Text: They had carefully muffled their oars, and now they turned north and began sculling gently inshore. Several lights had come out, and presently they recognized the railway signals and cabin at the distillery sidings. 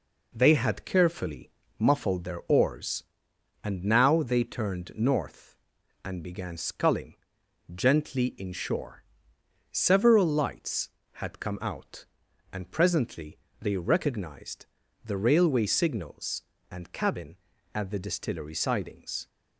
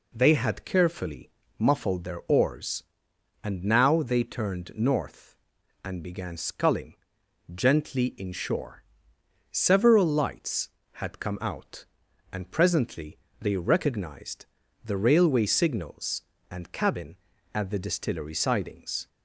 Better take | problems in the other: second | gets quieter; noticeable; throughout; 5 dB // pauses between "carefully" and "muffled"; slight; at 1.5 s; 0.28 s long; slight in the second // pauses between "sculling" and "gently"; noticeable; at 7.1 s; 0.60 s long; noticeable in the second // pauses between "presently" and "they"; slight; at 13.3 s; 0.22 s long; slight in the second // pauses between "recognized" and "the"; at 14.6 s; 0.38 s long; also in the second

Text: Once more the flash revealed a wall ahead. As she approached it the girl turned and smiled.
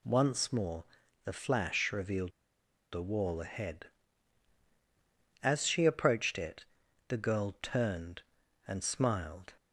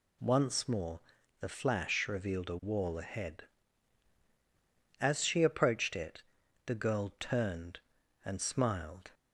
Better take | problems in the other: second | pauses between "more" and "the"; at 0.8 s; 0.40 s long; also in the second // pauses between "revealed" and "a"; noticeable; at 2.3 s; 0.62 s long // pauses between "it" and "the"; at 6.6 s; 0.44 s long; also in the second

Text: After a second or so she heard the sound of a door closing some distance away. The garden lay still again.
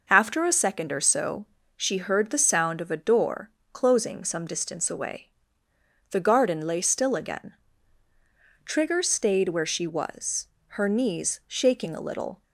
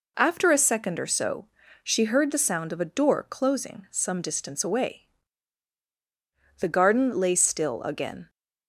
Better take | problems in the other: second | pauses between "so" and "she"; slight; at 1.4 s; 0.29 s long; slight in the second // pauses between "door" and "closing"; slight; at 3.4 s; 0.22 s long // goes on to say "Trigger stayed where she was her knees shaking a little"; strong; from 8.6 s on; 3.7 s long

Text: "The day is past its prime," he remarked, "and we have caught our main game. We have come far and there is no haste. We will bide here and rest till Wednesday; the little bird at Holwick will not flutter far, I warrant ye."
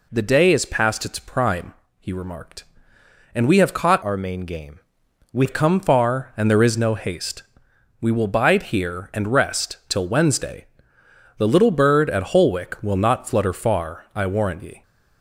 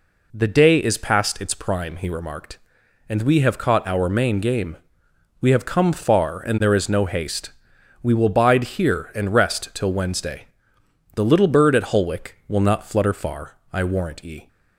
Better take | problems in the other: second | changes voice from "our" to "We"; from 4.0 to 5.4 s; 1.4 s long

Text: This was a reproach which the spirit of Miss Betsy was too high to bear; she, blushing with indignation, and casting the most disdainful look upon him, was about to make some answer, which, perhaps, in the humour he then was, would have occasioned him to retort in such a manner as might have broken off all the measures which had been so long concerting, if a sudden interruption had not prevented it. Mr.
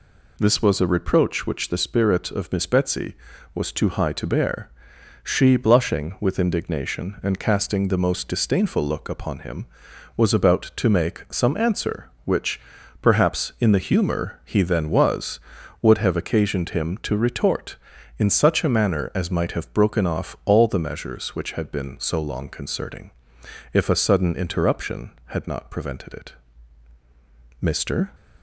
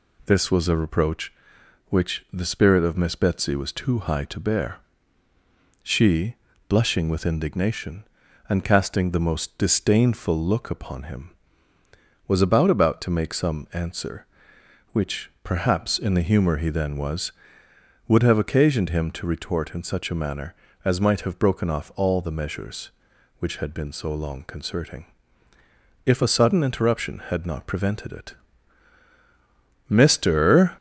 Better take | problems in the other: first | says "about" twice; at 12.7 s

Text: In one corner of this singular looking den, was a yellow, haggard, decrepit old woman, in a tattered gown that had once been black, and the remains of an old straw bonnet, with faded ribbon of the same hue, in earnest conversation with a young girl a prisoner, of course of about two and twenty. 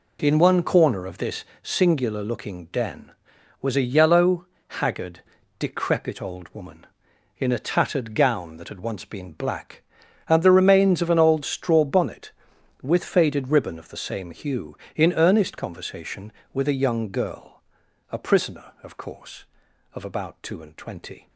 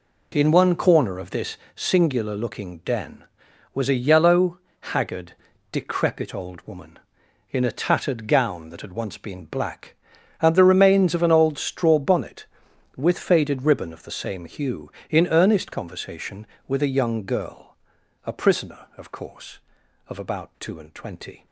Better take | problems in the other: neither | pauses between "this" and "singular"; slight; the same in both // pauses between "girl" and "a"; noticeable; the same in both

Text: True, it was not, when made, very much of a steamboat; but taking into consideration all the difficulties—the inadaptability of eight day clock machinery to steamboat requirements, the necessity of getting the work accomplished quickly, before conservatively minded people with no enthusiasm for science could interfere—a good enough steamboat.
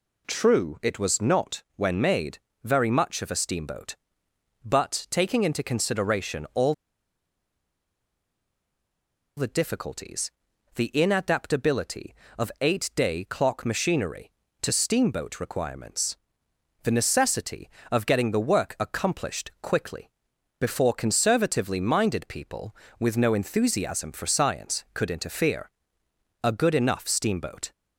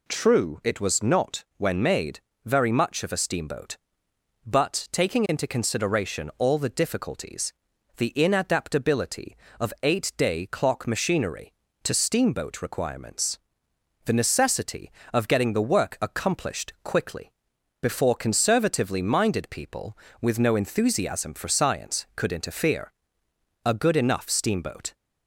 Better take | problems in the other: second | pauses between "all" and "the"; strong; at 6.7 s; 2.6 s long

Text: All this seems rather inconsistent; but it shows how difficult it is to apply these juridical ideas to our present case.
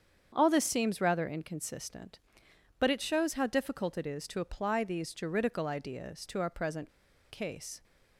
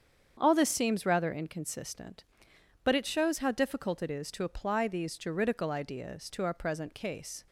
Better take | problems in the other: second | starts louder than the rest; strong; until 1.3 s; 7.5 dB; strong in the second // pauses between "present" and "case"; at 6.8 s; 0.40 s long

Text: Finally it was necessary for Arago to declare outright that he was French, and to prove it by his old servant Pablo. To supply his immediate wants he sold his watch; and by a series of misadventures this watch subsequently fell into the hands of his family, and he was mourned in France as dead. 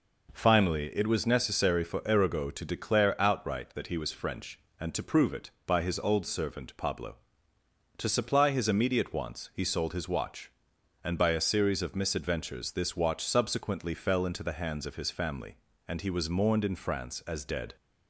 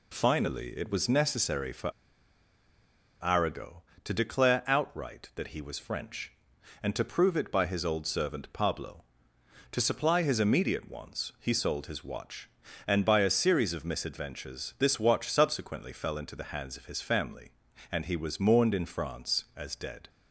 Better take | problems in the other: first | pauses between "for" and "Arago"; strong; at 1.9 s; 1.3 s long

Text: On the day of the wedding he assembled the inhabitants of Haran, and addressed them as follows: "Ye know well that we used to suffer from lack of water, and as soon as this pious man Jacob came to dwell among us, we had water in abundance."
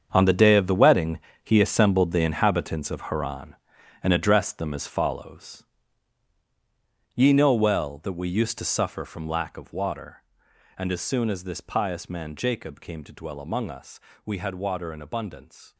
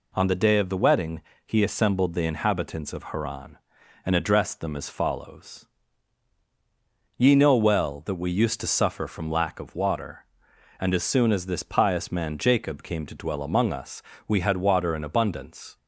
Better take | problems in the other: second | gets quieter; strong; throughout; 13.5 dB // pauses between "wedding" and "he"; slight; at 1.1 s; 0.26 s long; slight in the second

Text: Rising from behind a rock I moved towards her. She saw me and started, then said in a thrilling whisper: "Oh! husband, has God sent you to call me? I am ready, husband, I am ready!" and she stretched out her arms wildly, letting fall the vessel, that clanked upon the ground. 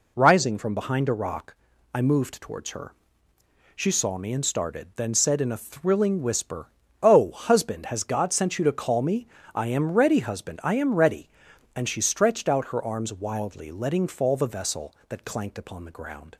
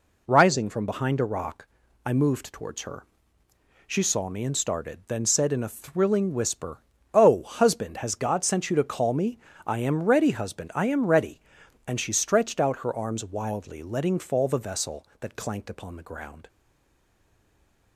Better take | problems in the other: first | pauses between "rock" and "I"; at 1.6 s; 0.38 s long; also in the first // stays silent after the last word; noticeable; from 16.4 s on; 1.5 s long

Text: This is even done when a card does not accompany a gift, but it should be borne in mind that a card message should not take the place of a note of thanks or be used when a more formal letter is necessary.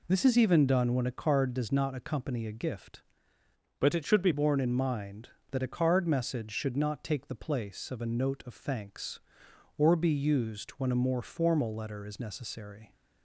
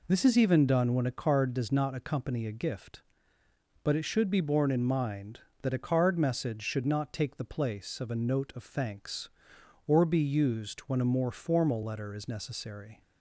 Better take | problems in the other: second | changes voice from "but" to "be"; from 3.8 to 4.3 s; 0.5 s long

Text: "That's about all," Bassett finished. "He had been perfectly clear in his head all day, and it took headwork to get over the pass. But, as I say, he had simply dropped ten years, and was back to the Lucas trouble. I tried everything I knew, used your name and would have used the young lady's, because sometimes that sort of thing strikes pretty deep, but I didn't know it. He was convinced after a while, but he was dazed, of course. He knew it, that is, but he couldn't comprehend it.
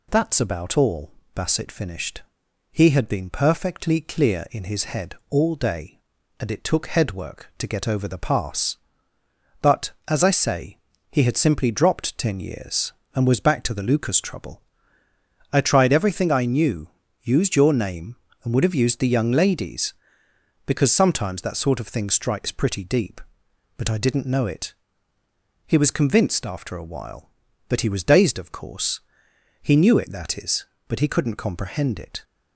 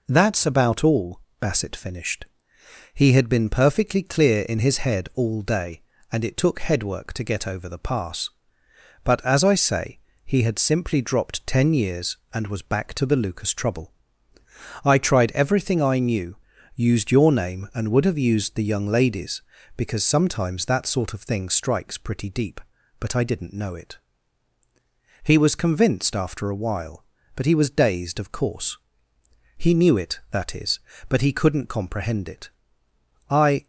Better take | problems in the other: first | goes on to say "I"; slight; from 33.2 s on; 0.36 s long

